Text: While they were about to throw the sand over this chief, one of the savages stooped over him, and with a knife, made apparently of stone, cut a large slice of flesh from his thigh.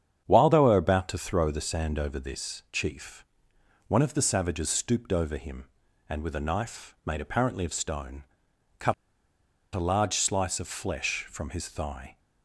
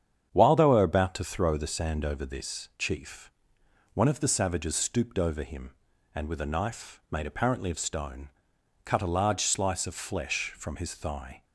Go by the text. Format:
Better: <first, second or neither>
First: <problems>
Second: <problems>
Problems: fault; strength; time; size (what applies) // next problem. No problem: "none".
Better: second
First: starts louder than the rest; strong; until 1.2 s; 8.5 dB // pauses between "cut" and "a"; noticeable; at 8.9 s; 0.79 s long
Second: starts louder than the rest; strong; until 1.3 s; 8.5 dB